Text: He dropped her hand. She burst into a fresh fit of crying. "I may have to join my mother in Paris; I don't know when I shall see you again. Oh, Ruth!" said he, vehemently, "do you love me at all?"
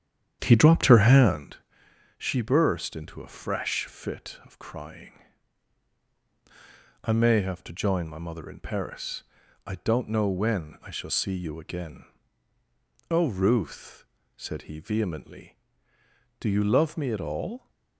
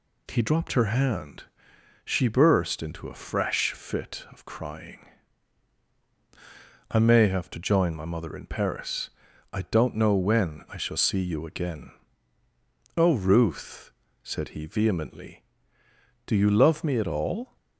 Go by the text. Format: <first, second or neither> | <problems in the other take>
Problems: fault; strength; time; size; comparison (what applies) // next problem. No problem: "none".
second | starts louder than the rest; strong; until 1.6 s; 9 dB